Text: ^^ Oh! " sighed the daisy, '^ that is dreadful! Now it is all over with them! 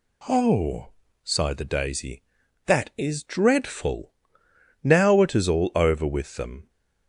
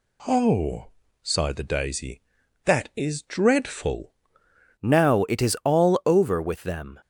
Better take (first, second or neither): first